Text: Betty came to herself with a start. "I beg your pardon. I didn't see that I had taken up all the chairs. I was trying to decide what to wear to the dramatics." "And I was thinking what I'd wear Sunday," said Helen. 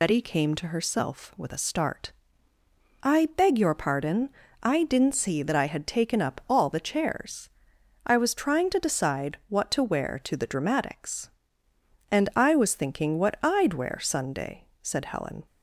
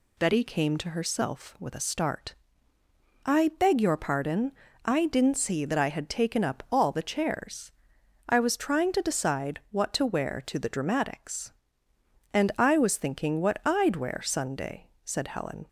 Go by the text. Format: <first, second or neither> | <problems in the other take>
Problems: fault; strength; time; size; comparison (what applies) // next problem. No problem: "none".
second | loses the start of "Betty"; at 0.0 s; 45 ms